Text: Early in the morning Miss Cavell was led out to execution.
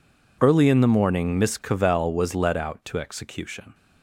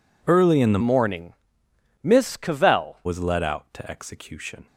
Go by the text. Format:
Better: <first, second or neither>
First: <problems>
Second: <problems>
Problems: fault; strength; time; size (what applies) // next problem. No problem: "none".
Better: first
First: none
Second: changes voice from "morning" to "Cavell"; from 0.7 to 2.9 s; 2.2 s long // pauses between "morning" and "Miss"; noticeable; at 1.3 s; 0.68 s long